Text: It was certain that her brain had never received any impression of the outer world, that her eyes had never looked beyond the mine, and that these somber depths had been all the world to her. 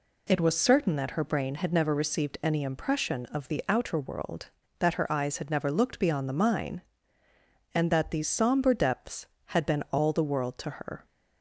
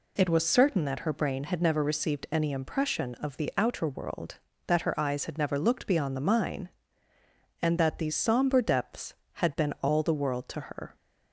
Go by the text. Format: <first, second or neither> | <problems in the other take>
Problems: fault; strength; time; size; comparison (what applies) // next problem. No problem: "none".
neither | none